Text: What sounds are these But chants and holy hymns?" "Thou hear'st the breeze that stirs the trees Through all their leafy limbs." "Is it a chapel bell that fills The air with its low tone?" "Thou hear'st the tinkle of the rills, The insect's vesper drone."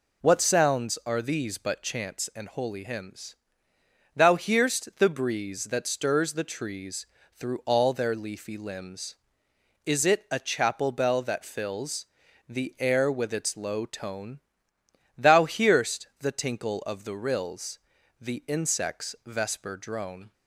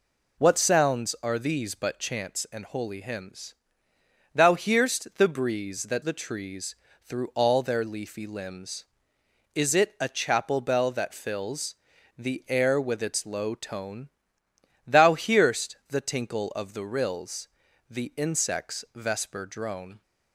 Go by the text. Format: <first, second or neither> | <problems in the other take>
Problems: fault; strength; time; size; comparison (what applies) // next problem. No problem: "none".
first | skips "stirs"; at 6.0 s // pauses between "trees" and "Through"; slight; at 6.7 s; 0.28 s long; slight in the first // pauses between "fills" and "The"; at 11.7 s; 0.42 s long; also in the first